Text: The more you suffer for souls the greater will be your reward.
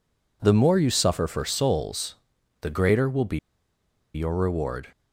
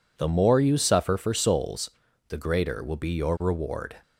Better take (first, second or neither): second